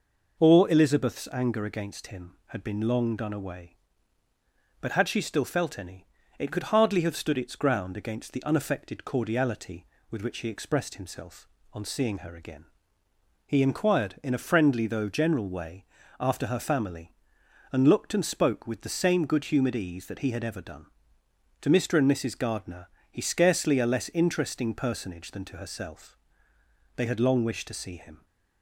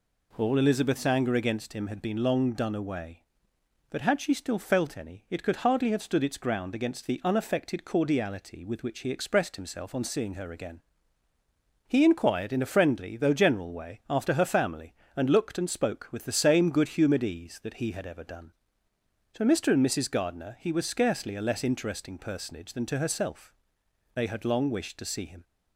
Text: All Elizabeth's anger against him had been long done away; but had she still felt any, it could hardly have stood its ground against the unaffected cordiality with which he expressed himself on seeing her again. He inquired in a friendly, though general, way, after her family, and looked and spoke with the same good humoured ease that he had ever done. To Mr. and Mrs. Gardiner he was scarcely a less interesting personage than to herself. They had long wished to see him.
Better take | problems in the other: second | pauses between "Gardiner" and "he"; slight; at 22.8 s; 0.24 s long // skips "was"; at 23.2 s

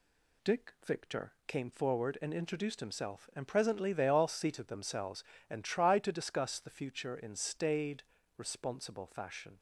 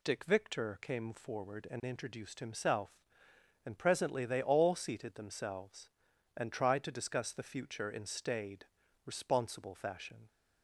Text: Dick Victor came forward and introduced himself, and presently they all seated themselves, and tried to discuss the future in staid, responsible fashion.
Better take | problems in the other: neither | none

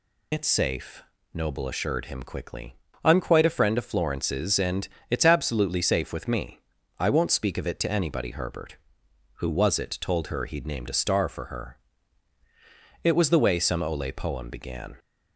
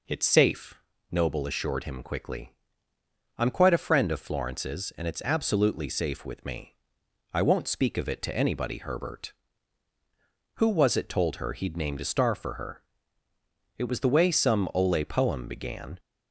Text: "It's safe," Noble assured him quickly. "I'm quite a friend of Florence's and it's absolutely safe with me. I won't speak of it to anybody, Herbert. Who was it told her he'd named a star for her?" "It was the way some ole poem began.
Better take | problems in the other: second | loses the start of "It's"; at 0.3 s; 55 ms // pauses between "and" and "it's"; slight; at 4.8 s; 0.22 s long

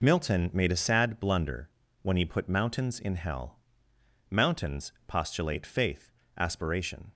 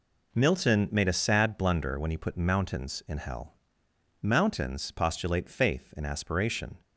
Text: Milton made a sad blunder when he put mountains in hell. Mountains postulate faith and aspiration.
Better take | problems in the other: second | pauses between "blunder" and "when"; slight; at 1.7 s; 0.32 s long // pauses between "Mountains" and "postulate"; slight; at 4.9 s; 0.16 s long // skips "and"; at 6.2 s

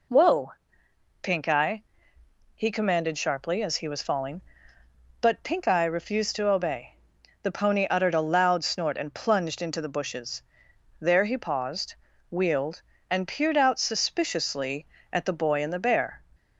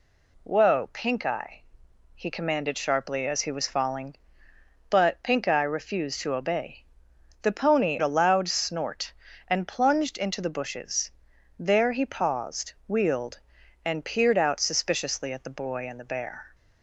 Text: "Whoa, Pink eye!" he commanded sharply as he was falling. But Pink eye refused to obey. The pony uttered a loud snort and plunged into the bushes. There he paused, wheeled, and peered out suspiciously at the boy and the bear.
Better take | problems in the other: first | skips "uttered"; at 8.0 s

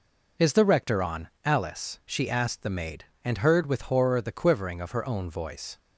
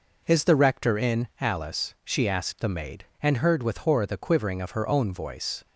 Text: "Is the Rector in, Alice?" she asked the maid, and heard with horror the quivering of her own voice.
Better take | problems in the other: second | says "on" for "in"; at 1.0 s

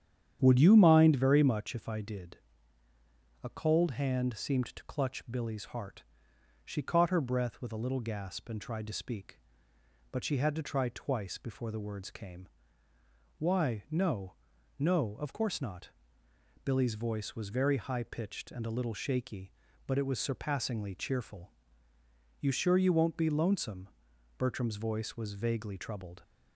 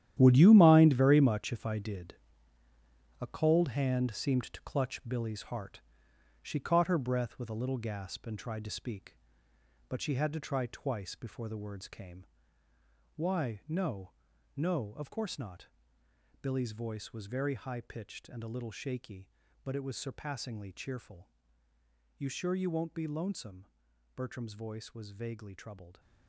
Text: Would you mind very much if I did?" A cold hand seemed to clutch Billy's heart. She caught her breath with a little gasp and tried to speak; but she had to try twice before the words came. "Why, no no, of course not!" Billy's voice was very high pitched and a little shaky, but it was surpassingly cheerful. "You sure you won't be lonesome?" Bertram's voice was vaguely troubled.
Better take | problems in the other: first | gets quieter; strong; throughout; 11.5 dB // starts louder than the rest; strong; until 1.2 s; 11.5 dB; strong in the first // pauses between "no" and "no"; noticeable; at 14.0 s; 0.46 s long; noticeable in the first

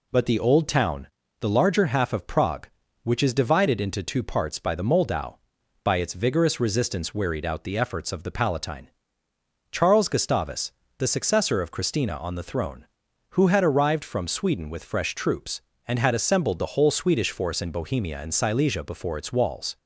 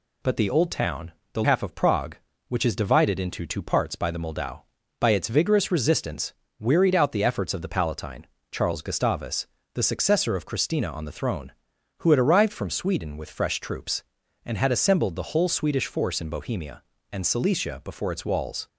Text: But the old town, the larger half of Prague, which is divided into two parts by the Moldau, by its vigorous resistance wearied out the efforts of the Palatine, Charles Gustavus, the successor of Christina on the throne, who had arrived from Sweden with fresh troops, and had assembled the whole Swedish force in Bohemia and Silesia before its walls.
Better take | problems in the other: first | skips "larger"; at 1.4 s // pauses between "resistance" and "wearied"; slight; at 6.3 s; 0.26 s long

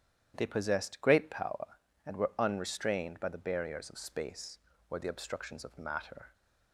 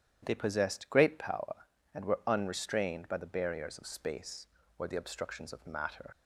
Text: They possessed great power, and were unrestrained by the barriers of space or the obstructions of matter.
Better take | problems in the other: first | starts louder than the rest; strong; until 1.2 s; 10 dB; strong in the first // leaves "matter" unfinished; at 6.1 s; 90 ms

